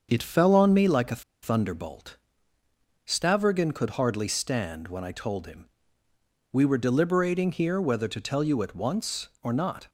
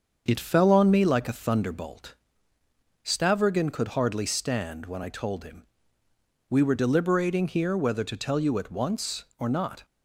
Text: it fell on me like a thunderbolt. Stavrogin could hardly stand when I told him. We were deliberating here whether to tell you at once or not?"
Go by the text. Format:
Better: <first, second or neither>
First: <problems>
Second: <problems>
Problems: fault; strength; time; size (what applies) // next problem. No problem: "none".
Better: second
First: starts louder than the rest; until 1.1 s; 6.5 dB // pauses between "a" and "thunderbolt"; slight; at 1.2 s; 0.20 s long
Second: starts louder than the rest; until 1.2 s; 6.5 dB